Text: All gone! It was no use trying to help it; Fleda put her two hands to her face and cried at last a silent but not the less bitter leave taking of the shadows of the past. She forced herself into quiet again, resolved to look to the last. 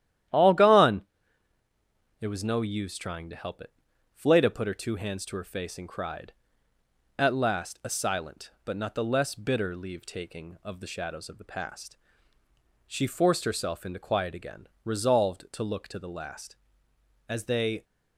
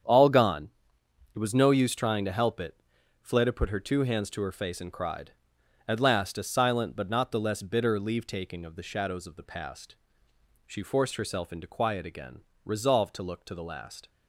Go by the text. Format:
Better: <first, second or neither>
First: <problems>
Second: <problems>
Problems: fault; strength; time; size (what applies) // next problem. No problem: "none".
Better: second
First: starts louder than the rest; strong; until 2.4 s; 11.5 dB // goes on to say "As they"; from 17.2 s on; 0.58 s long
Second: starts louder than the rest; strong; until 1.7 s; 8 dB